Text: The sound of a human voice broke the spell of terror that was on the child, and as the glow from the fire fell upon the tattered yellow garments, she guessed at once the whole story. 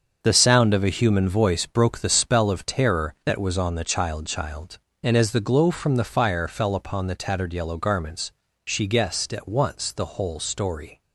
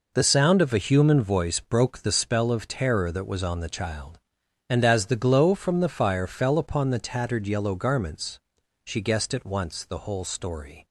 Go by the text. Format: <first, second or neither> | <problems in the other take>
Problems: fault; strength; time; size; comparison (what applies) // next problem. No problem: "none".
second | starts louder than the rest; until 1.2 s; 7 dB // says "child" twice; at 4.2 s